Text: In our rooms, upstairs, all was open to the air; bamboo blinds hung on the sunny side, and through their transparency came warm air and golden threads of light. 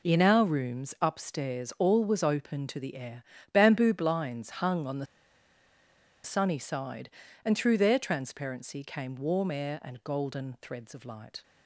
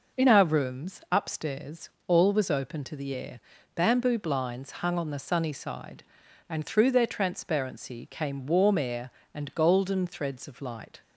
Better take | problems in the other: second | pauses between "the" and "sunny"; at 5.0 s; 1.1 s long

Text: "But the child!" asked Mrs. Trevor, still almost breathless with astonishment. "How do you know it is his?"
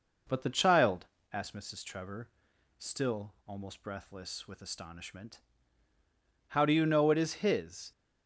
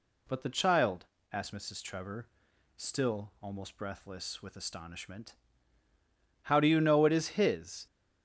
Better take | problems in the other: second | starts louder than the rest; noticeable; until 1.5 s; 5 dB

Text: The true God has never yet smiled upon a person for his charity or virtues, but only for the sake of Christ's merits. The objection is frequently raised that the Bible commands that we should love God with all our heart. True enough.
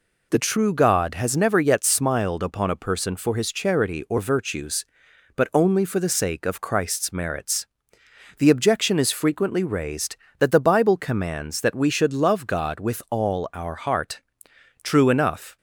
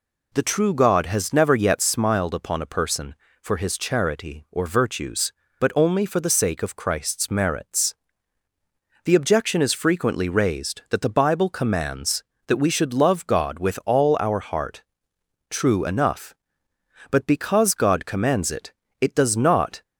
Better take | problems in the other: first | goes on to say "But because God commands it it does not"; strong; from 17.0 s on; 2.7 s long

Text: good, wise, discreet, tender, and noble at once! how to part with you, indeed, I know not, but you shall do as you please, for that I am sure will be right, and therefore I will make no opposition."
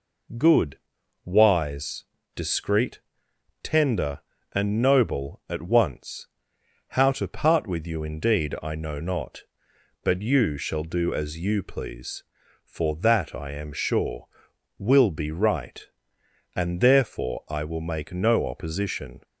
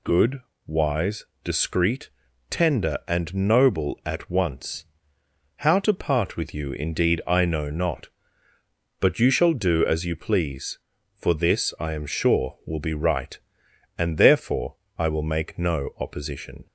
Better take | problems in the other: first | says "this" for "that"; at 11.3 s // pauses between "therefore" and "I"; slight; at 14.7 s; 0.22 s long

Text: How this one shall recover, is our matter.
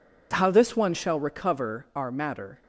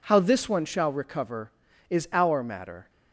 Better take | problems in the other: second | skips "is"; at 1.8 s

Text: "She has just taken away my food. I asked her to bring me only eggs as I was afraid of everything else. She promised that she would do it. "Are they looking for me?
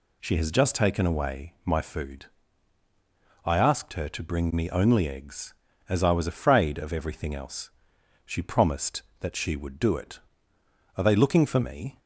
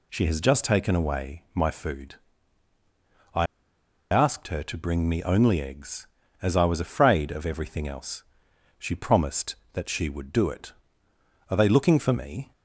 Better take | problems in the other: first | pauses between "I" and "asked"; noticeable; at 3.4 s; 0.65 s long

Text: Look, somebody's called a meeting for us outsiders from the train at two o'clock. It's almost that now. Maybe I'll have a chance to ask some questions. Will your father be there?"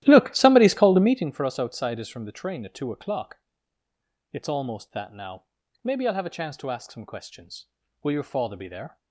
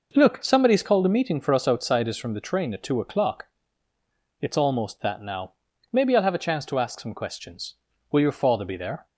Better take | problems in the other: second | starts louder than the rest; strong; until 1.4 s; 14 dB

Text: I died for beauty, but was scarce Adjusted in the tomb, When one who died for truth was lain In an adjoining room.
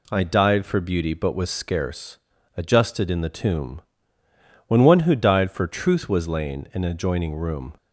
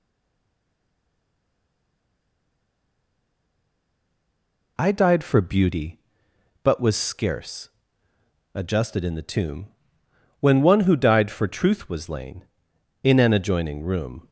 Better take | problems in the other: first | stays silent before the first word; strong; until 4.7 s; 4.7 s long // pauses between "scarce" and "Adjusted"; noticeable; at 7.7 s; 0.84 s long; also in the first

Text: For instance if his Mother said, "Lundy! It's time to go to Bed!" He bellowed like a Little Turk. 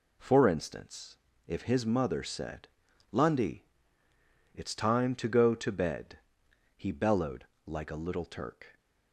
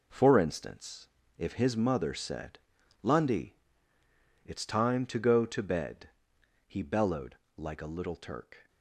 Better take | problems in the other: first | gets quieter; strong; throughout; 8.5 dB // pauses between "instance" and "if"; slight; at 1.0 s; 0.30 s long; slight in the first // pauses between "bellowed" and "like"; slight; at 7.3 s; 0.18 s long; slight in the first

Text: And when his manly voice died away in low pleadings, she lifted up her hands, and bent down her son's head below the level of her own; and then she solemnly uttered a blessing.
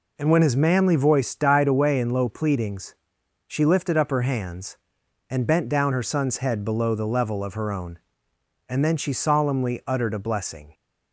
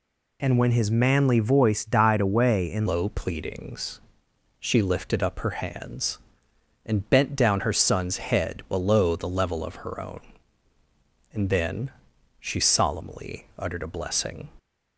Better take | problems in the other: first | changes voice at "low"; from 2.8 s on; 11.6 s long // pauses between "then" and "she"; noticeable; at 11.9 s; 0.48 s long

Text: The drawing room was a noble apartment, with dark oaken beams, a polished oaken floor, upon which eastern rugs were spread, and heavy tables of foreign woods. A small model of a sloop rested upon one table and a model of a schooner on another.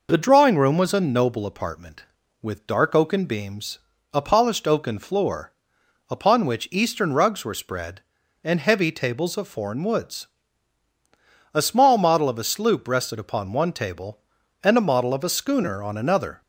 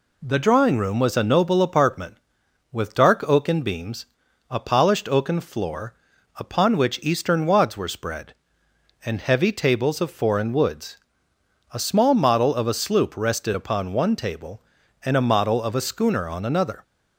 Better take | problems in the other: first | says "wads" for "rugs"; at 7.4 s

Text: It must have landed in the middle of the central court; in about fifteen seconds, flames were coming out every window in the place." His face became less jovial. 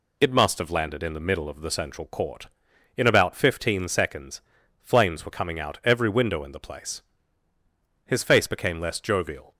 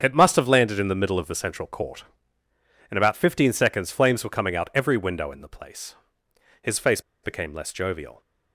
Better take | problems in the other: first | starts louder than the rest; strong; until 1.0 s; 7 dB // pauses between "face" and "became"; slight; at 7.0 s; 0.21 s long

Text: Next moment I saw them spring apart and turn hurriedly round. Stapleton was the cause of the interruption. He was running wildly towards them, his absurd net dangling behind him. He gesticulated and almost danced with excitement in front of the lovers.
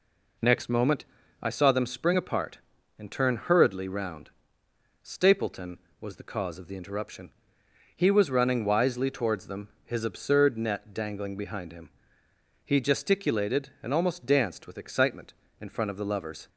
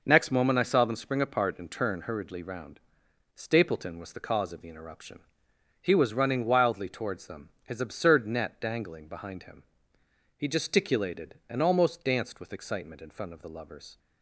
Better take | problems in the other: second | pauses between "moment" and "I"; at 1.0 s; 0.38 s long // says "wisely" for "wildly"; at 8.6 s

